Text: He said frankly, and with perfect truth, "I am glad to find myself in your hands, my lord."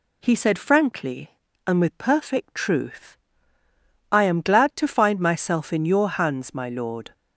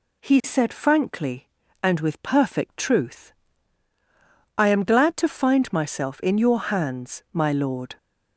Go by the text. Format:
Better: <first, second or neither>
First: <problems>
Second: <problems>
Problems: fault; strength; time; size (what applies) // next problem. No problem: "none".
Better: neither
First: none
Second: none